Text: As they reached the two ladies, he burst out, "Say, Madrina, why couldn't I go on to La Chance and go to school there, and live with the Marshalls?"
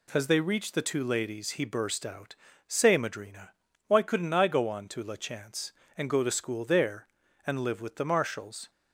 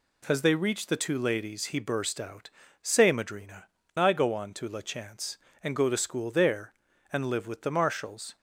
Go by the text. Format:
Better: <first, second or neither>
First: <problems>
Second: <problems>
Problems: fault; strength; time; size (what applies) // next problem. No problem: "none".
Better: first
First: none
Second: skips "why couldn't"; at 3.8 s